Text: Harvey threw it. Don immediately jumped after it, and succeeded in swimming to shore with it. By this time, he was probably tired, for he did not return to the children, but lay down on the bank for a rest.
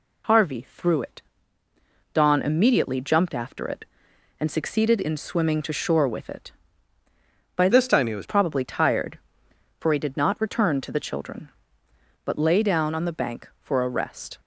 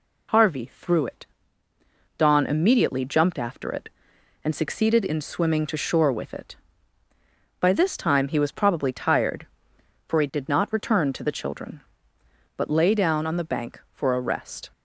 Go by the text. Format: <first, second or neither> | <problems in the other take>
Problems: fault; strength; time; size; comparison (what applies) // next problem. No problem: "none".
second | changes voice from "this" to "was"; from 7.7 to 8.2 s; 0.5 s long